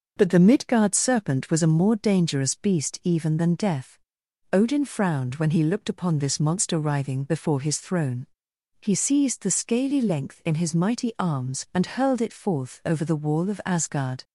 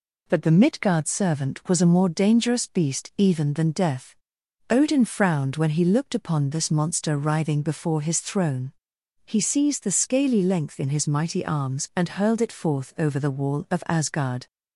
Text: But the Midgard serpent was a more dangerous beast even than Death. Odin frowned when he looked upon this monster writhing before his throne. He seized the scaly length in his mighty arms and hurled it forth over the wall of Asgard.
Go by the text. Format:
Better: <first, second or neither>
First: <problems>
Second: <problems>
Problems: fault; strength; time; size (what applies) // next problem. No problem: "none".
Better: first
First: none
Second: says "servant" for "serpent"; at 1.0 s